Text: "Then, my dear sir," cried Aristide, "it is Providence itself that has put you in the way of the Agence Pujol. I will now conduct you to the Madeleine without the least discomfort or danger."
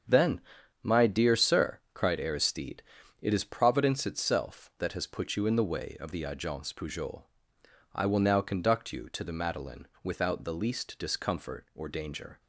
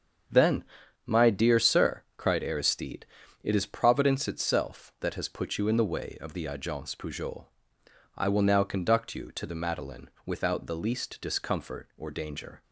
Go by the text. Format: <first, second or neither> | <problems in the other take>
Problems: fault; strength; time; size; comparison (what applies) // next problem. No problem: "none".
neither | starts louder than the rest; strong; the same in both // pauses between "Madeleine" and "without"; slight; the same in both